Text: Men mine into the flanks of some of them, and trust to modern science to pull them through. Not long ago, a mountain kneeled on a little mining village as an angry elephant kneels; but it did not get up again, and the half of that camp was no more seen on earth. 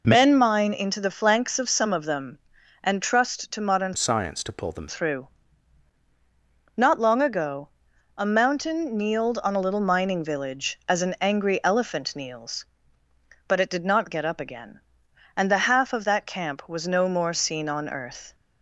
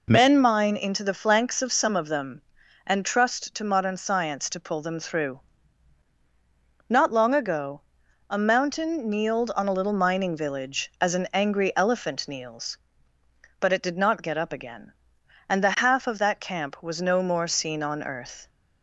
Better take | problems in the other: second | changes voice from "science" to "them"; from 3.9 to 4.8 s; 0.9 s long

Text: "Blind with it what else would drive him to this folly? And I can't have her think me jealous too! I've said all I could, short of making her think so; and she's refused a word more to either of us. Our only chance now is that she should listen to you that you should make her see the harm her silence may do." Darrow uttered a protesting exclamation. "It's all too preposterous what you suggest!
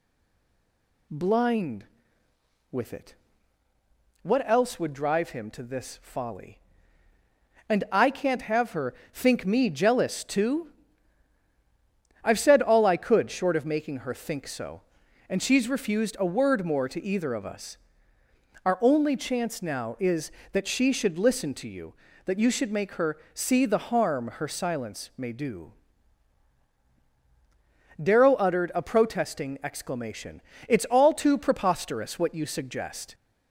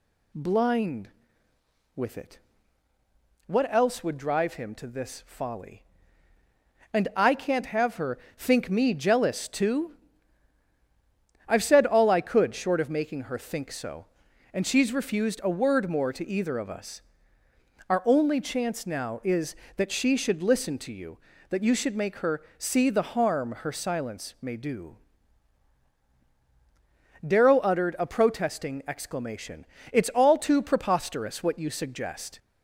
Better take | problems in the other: second | stays silent before the first word; until 1.0 s; 1.0 s long // pauses between "it" and "what"; at 3.1 s; 1.0 s long; also in the second // pauses between "her" and "think"; slight; at 8.9 s; 0.22 s long; slight in the second // pauses between "her" and "see"; slight; at 23.1 s; 0.18 s long; slight in the second

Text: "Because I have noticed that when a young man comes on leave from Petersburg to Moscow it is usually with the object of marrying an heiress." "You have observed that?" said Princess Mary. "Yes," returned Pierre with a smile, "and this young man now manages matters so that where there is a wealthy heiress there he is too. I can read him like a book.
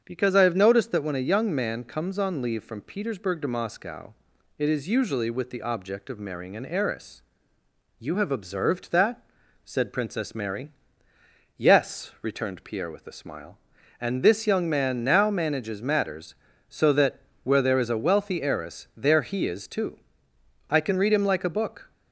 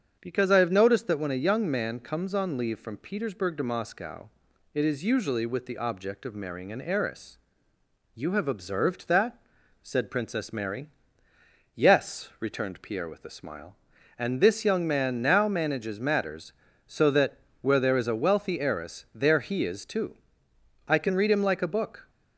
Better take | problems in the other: neither | starts louder than the rest; strong; the same in both // pauses between "Moscow" and "it"; the same in both // pauses between "that" and "where"; slight; the same in both

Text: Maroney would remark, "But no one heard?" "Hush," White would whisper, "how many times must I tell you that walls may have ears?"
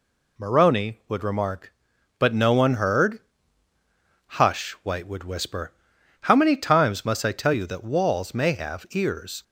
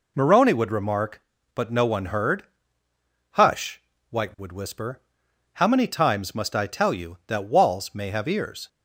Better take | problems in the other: neither | none

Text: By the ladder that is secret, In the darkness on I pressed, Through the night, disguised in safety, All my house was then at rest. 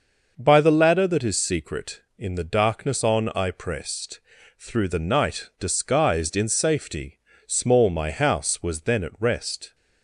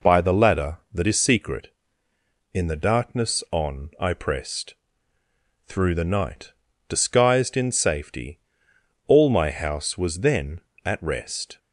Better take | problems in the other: second | starts louder than the rest; noticeable; until 1.3 s; 6 dB // says "Small" for "All"; at 7.4 s

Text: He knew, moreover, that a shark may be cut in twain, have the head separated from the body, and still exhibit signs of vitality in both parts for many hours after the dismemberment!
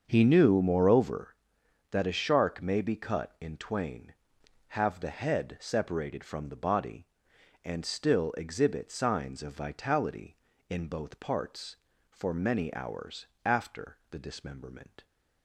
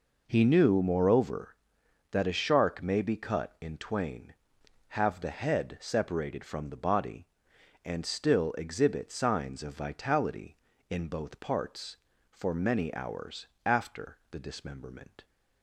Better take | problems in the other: second | starts louder than the rest; until 1.2 s; 7 dB // pauses between "hours" and "after"; slight; at 13.2 s; 0.18 s long; slight in the second

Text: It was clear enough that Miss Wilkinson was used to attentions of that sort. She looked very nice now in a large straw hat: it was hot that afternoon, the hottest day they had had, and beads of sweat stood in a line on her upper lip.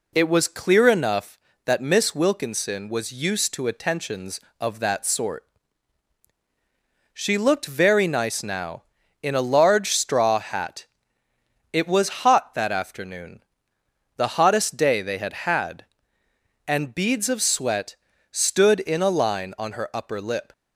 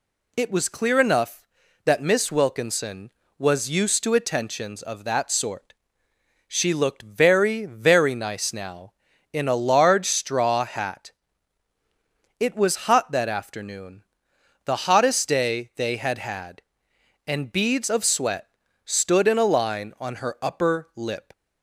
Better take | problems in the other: first | says "very" twice; at 7.6 s // pauses between "sweat" and "stood"; at 18.4 s; 0.38 s long; slight in the first

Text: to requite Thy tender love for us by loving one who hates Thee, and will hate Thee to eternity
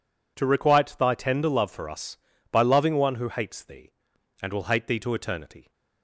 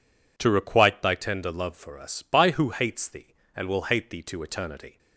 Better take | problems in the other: first | skips "loving one"; at 2.5 s

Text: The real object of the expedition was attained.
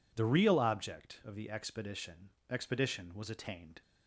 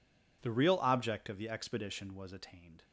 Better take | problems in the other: second | says "expedition" twice; at 2.4 s

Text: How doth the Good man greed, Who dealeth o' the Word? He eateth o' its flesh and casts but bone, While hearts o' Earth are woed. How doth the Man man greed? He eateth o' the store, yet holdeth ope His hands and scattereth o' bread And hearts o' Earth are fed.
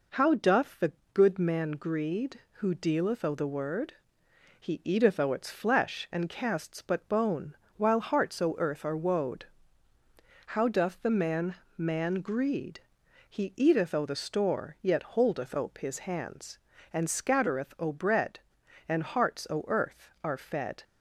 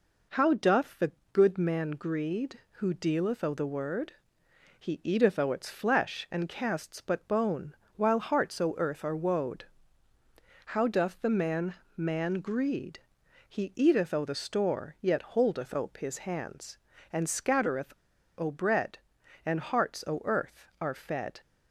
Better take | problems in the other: first | pauses between "the" and "Good"; slight; at 1.0 s; 0.22 s long; slight in the first // pauses between "Man" and "man"; slight; at 11.7 s; 0.22 s long; slight in the first // pauses between "scattereth" and "o"; at 17.9 s; 0.45 s long

